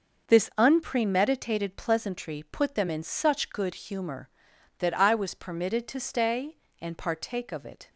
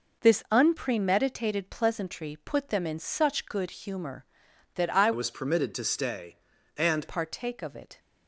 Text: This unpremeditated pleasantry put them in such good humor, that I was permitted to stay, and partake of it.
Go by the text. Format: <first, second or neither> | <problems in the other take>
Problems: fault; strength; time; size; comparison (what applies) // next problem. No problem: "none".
first | changes voice from "was" to "and"; from 5.1 to 7.0 s; 1.9 s long